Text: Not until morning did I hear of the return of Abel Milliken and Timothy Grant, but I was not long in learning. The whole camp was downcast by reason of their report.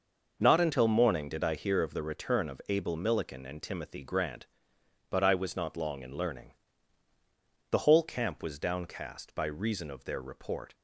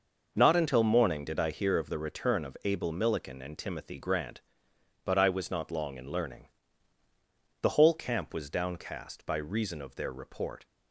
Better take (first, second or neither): neither